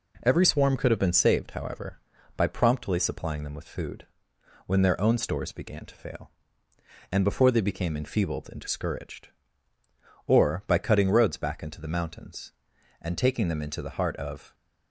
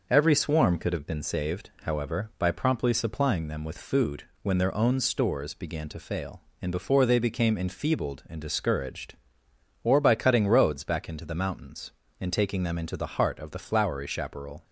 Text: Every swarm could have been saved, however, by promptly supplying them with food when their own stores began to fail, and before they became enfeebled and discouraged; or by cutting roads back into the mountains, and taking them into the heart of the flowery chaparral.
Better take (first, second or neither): second